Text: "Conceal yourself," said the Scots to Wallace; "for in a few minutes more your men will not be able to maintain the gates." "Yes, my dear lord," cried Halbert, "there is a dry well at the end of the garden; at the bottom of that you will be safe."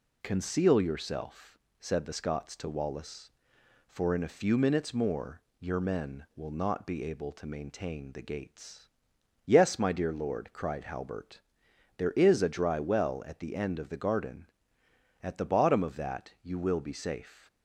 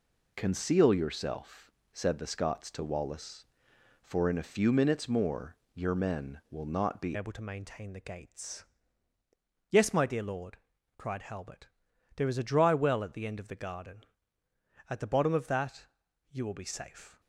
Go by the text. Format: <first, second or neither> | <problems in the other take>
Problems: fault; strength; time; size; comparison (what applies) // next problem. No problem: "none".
first | pauses between "more" and "your"; slight; at 5.5 s; 0.22 s long; slight in the first // changes voice at "able"; from 7.1 s on; 10.0 s long // pauses between "that" and "you"; noticeable; at 15.8 s; 0.46 s long